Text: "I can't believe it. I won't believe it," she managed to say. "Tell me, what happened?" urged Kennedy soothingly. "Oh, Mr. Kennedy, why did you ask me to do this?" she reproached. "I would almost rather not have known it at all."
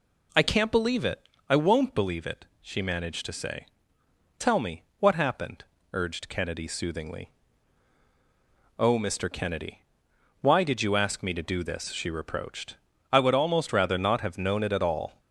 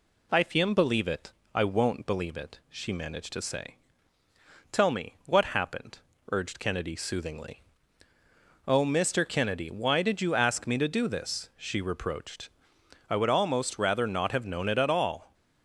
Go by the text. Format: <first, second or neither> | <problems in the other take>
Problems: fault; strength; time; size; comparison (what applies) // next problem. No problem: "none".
first | says "fiem" for "can't"; at 0.4 s